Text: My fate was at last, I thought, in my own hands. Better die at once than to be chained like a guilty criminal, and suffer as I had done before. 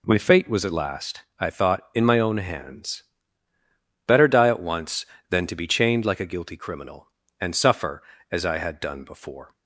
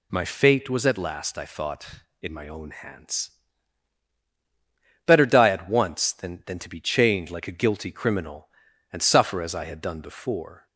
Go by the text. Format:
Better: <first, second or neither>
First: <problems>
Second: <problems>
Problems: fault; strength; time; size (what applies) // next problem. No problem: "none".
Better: first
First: none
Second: says "than" twice; at 6.4 s